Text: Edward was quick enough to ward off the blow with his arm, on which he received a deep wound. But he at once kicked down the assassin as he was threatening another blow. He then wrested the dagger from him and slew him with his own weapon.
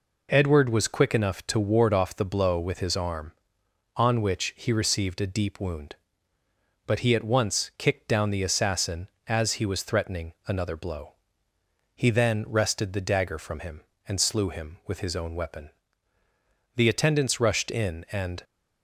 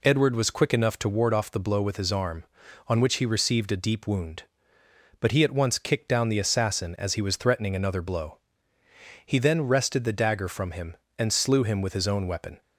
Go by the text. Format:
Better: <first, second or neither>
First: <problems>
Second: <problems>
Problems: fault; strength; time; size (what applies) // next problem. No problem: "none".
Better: second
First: goes on to say "The attendants rushed in and"; from 16.7 s on; 1.6 s long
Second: none